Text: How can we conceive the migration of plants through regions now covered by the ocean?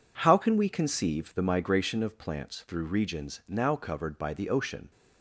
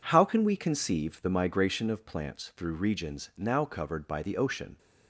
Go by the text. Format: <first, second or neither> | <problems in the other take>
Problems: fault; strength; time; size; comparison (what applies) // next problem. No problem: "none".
neither | none